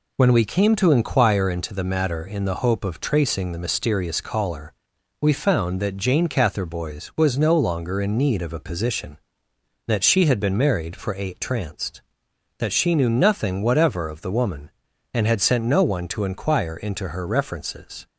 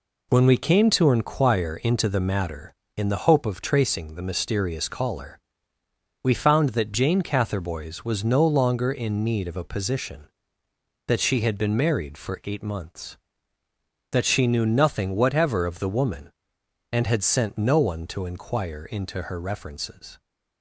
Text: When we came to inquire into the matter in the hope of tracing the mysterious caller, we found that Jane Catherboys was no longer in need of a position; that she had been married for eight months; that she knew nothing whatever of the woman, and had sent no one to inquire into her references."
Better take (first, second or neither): second